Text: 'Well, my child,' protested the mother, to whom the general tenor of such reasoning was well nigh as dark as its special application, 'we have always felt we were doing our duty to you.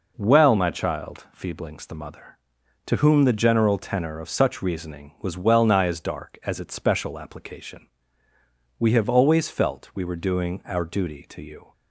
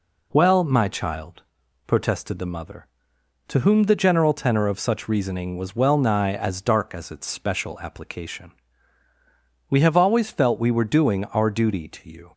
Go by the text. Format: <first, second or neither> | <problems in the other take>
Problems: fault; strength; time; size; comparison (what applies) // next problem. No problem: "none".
second | says "feeblings" for "protested"; at 1.3 s